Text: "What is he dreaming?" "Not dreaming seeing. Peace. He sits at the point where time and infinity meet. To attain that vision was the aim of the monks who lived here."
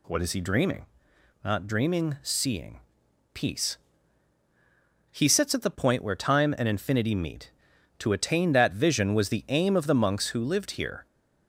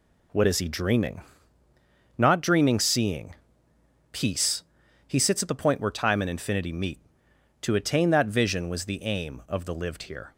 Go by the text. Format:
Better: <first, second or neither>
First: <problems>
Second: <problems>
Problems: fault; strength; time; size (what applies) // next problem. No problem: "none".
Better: first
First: none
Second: skips "monks who"; at 9.7 s